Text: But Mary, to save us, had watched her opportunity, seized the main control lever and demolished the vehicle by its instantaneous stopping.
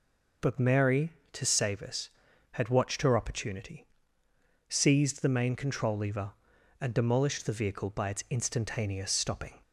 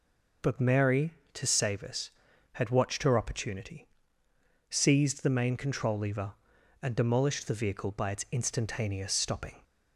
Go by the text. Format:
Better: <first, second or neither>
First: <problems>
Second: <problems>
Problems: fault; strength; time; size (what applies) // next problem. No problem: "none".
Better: neither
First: none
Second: none